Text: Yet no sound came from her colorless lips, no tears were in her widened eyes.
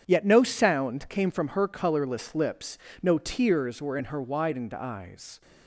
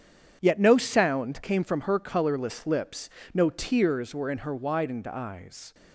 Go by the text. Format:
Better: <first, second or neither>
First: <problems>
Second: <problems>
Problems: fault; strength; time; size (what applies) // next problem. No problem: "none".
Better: neither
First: starts louder than the rest; strong; until 1.0 s; 8.5 dB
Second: starts louder than the rest; strong; until 1.4 s; 8.5 dB